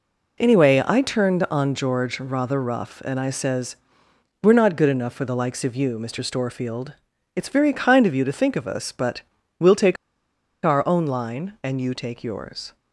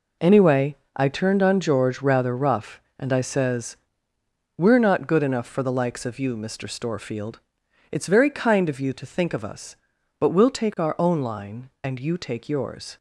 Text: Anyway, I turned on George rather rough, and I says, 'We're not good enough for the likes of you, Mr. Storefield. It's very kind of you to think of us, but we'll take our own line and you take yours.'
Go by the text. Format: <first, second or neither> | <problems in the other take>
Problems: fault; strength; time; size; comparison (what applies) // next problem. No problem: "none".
second | pauses between "but" and "we'll"; at 9.2 s; 0.38 s long // pauses between "take" and "our"; noticeable; at 9.9 s; 0.69 s long